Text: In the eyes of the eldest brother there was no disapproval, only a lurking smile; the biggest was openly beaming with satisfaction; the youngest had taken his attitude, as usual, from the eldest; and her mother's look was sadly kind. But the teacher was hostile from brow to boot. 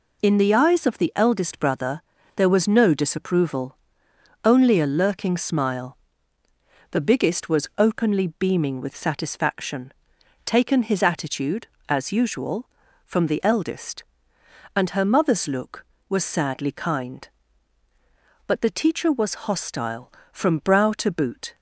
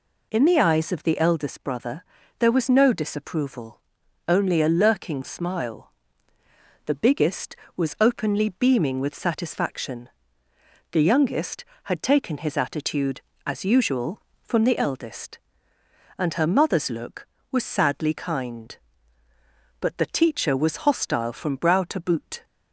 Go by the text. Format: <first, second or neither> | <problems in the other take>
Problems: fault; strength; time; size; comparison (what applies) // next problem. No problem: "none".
second | pauses between "brother" and "there"; slight; at 2.0 s; 0.34 s long; slight in the second // skips "the youngest had"; at 10.1 s